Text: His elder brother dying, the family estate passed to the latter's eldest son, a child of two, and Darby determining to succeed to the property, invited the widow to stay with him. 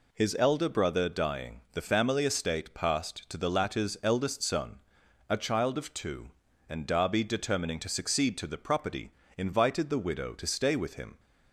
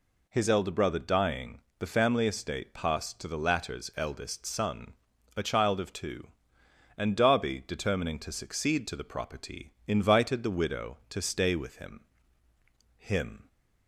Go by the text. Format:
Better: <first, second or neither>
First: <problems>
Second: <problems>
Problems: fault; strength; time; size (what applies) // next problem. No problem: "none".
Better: first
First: none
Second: says "him" twice; at 12.9 s